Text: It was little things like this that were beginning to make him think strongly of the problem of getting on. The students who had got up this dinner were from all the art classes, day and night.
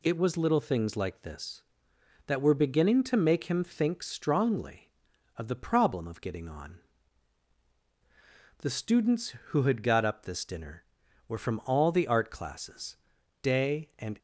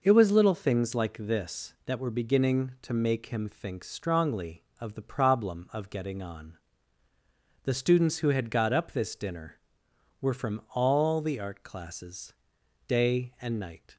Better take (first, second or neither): second